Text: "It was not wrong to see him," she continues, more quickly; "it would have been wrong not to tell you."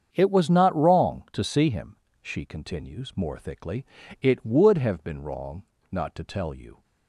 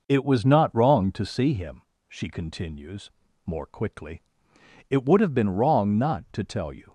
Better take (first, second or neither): second